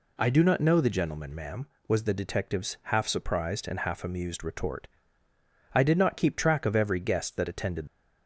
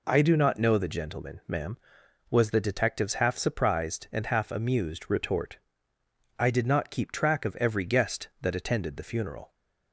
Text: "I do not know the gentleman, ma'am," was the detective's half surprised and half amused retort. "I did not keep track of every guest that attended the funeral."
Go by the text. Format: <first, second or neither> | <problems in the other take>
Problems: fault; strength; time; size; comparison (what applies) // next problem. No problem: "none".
second | stops before "the funeral"; at 7.8 s